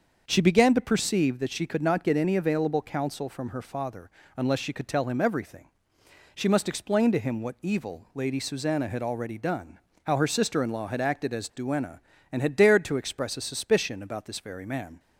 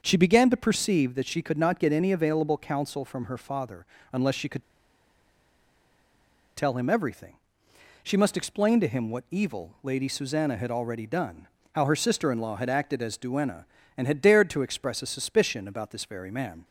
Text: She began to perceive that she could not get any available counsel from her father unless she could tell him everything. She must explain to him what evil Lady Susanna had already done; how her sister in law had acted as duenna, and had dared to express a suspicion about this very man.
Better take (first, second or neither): first